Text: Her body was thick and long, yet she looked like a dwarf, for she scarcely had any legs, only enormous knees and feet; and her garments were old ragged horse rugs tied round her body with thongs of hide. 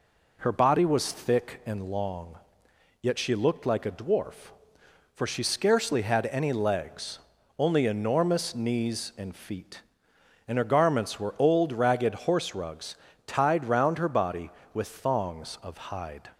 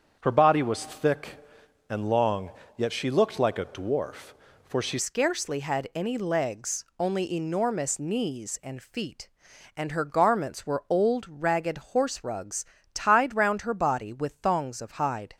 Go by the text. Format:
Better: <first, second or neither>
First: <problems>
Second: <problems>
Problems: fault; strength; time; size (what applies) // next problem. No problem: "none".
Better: first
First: pauses between "rugs" and "tied"; slight; at 12.9 s; 0.30 s long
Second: starts louder than the rest; strong; until 1.2 s; 7.5 dB // changes voice at "scarcely"; from 4.9 s on; 10.4 s long // pauses between "ragged" and "horse"; slight; at 11.7 s; 0.16 s long // pauses between "rugs" and "tied"; slight; at 12.6 s; 0.30 s long